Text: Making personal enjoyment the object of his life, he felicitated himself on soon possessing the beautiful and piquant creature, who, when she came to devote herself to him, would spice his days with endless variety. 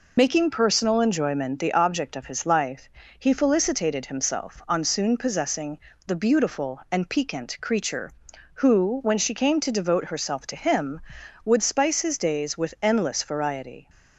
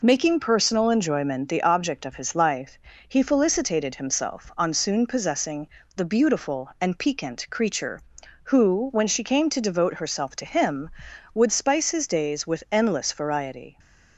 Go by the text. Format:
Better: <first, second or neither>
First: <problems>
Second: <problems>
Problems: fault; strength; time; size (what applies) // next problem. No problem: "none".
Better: second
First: loses the start of "Making"; at 0.1 s; 40 ms // pauses between "possessing" and "the"; slight; at 5.7 s; 0.26 s long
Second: pauses between "possessing" and "the"; slight; at 5.6 s; 0.26 s long